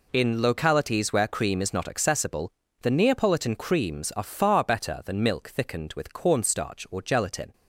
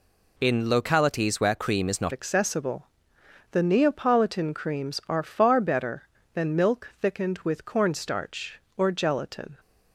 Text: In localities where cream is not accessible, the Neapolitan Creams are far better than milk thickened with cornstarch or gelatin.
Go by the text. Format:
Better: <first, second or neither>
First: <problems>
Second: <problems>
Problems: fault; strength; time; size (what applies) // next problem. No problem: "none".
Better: first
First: none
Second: changes voice at "accessible"; from 2.1 s on; 7.4 s long